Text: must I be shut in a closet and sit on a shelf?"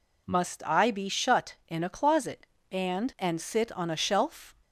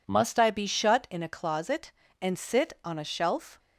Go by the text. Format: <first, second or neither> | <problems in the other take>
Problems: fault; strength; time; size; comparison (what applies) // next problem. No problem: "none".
second | says "and" twice; at 3.1 s